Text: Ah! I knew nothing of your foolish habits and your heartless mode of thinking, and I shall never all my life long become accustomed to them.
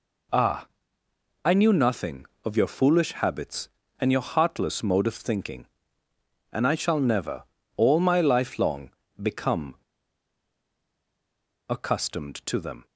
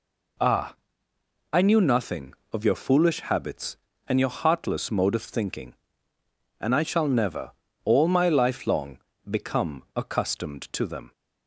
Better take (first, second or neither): second